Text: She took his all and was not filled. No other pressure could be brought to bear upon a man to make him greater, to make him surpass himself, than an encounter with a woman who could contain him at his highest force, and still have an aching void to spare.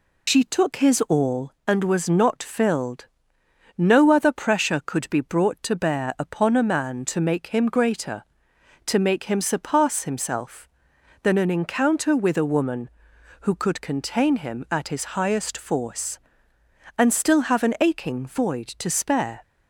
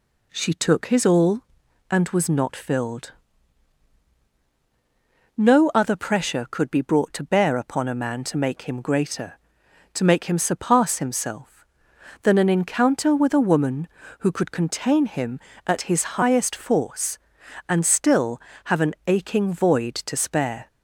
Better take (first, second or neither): second